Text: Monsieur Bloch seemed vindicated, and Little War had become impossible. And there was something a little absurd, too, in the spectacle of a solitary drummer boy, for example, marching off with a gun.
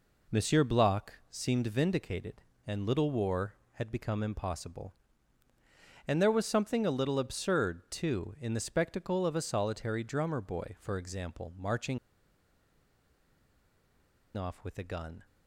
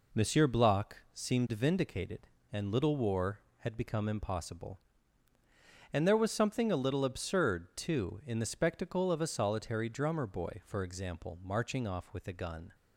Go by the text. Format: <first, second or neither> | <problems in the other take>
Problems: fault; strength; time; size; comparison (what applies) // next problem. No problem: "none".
second | pauses between "Bloch" and "seemed"; slight; at 1.1 s; 0.18 s long; slight in the second // pauses between "marching" and "off"; strong; at 11.9 s; 2.3 s long